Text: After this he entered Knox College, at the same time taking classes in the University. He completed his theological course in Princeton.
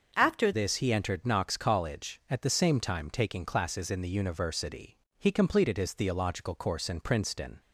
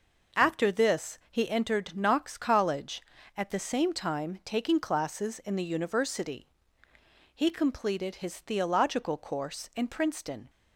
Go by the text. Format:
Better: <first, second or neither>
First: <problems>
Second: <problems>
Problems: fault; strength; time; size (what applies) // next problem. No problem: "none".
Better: second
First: starts louder than the rest; until 1.1 s; 6.5 dB // changes voice at "this"; from 0.5 s on; 7.0 s long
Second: none